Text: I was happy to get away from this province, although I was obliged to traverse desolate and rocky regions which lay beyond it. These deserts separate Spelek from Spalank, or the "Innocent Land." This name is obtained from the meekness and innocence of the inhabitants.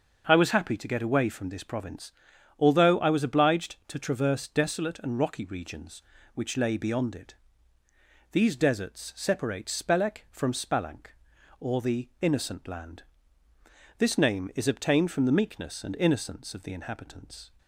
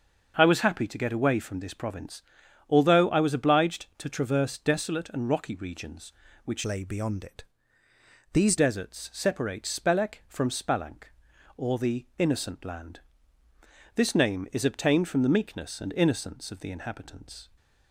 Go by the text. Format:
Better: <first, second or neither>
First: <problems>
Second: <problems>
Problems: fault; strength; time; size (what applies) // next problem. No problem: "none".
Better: first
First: starts louder than the rest; until 1.3 s; 6 dB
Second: starts louder than the rest; until 1.3 s; 6.5 dB // changes voice from "lay" to "These"; from 6.6 to 8.5 s; 1.9 s long